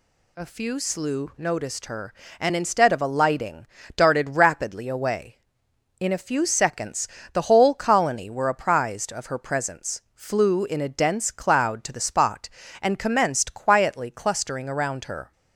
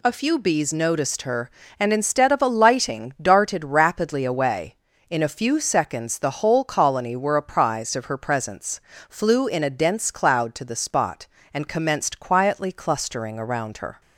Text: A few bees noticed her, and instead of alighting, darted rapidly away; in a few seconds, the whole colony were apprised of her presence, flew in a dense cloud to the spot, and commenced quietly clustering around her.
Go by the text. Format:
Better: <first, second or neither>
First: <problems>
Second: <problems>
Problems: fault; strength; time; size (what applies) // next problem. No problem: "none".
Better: second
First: says "slew" for "bees"; at 0.7 s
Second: none